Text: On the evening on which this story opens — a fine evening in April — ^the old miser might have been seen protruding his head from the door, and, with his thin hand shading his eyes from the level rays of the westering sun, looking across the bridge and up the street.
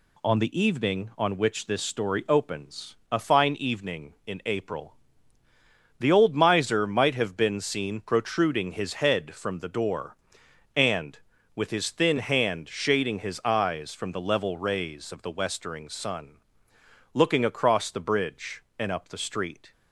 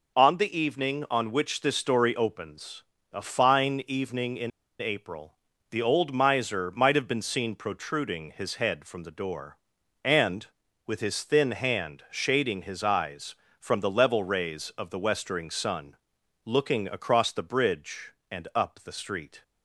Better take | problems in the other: first | pauses between "in" and "April"; slight; at 4.5 s; 0.30 s long

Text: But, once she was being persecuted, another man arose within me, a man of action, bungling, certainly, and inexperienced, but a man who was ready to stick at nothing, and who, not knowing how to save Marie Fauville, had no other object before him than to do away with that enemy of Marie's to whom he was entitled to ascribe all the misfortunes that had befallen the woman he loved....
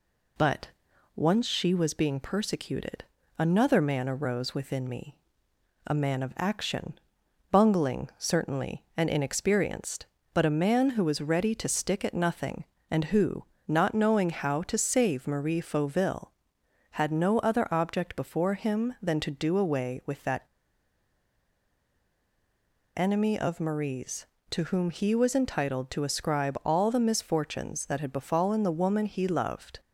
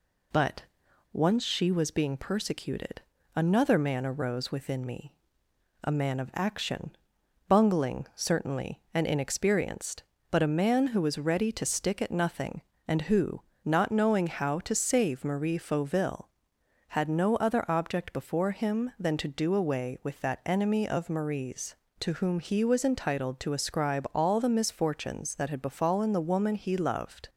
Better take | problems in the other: second | pauses between "that" and "enemy"; strong; at 20.4 s; 2.5 s long

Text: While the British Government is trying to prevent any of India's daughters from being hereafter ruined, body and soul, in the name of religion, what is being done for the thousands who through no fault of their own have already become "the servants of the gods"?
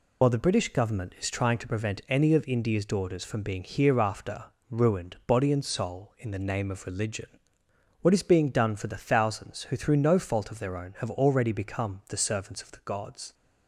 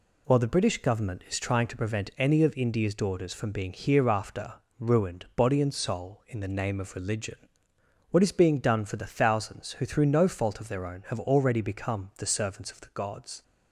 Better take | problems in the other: second | loses the start of "While"; at 0.2 s; 40 ms // pauses between "hereafter" and "ruined"; slight; at 4.4 s; 0.24 s long; slight in the second

